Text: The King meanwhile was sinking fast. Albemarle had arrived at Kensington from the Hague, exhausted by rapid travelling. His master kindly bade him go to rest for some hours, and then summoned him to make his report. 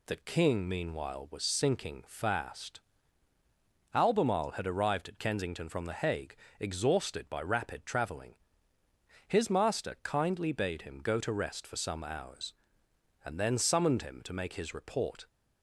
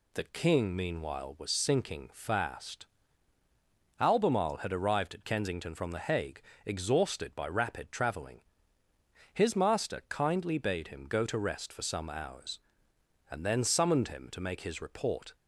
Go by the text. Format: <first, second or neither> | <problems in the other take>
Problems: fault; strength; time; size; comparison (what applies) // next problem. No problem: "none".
neither | none